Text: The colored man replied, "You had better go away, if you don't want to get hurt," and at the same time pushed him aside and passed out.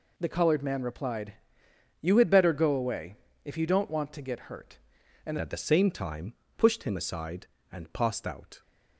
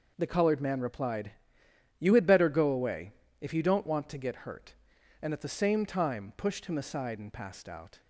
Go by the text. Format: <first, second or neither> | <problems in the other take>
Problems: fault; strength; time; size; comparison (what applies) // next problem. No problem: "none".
second | changes voice at "at"; from 5.3 s on; 3.3 s long // pauses between "time" and "pushed"; slight; at 6.3 s; 0.24 s long